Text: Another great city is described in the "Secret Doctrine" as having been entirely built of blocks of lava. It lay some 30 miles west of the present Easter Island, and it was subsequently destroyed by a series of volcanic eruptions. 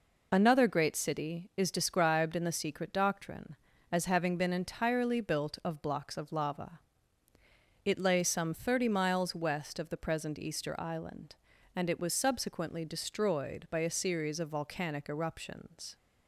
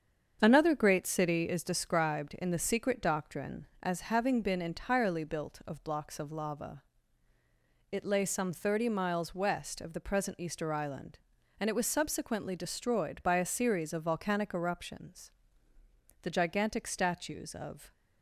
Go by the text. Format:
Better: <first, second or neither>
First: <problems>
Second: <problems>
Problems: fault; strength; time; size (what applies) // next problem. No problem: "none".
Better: first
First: none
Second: starts louder than the rest; strong; until 1.4 s; 7.5 dB // goes on to say "The gigantic statues of"; strong; from 16.2 s on; 1.7 s long